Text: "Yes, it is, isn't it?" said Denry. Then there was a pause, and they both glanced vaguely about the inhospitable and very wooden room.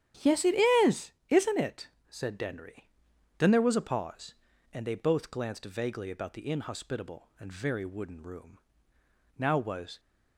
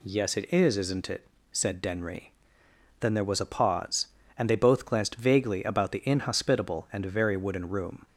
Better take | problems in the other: second | starts louder than the rest; until 1.7 s; 7 dB // goes on to say "Now was"; noticeable; from 9.3 s on; 0.62 s long

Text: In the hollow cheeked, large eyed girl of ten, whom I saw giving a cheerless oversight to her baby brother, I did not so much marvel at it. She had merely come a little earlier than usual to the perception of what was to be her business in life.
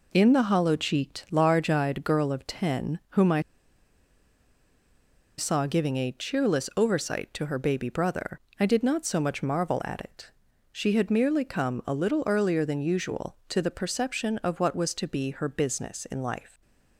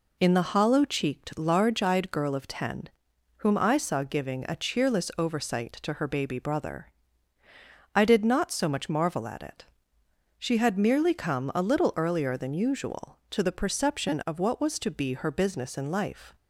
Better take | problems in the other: second | pauses between "I" and "saw"; strong; at 3.3 s; 1.9 s long

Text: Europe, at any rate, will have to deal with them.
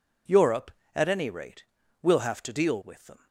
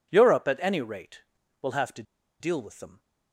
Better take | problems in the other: first | pauses between "to" and "deal"; at 2.0 s; 0.37 s long

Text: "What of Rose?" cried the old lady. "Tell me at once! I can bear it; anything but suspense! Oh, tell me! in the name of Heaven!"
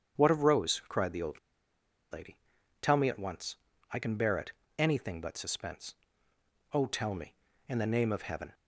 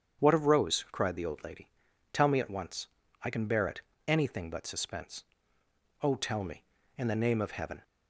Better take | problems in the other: second | starts louder than the rest; strong; until 1.2 s; 8 dB; strong in the second // pauses between "old" and "lady"; noticeable; at 1.3 s; 0.74 s long

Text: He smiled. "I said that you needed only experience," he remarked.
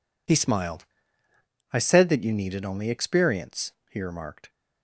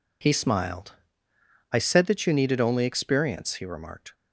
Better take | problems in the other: neither | none

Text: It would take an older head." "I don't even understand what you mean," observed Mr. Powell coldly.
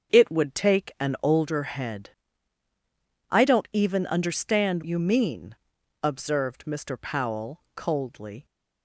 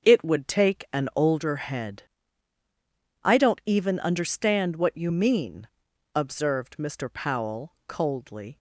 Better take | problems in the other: second | starts louder than the rest; until 1.2 s; 6.5 dB; also in the second // skips "what"; at 4.8 s

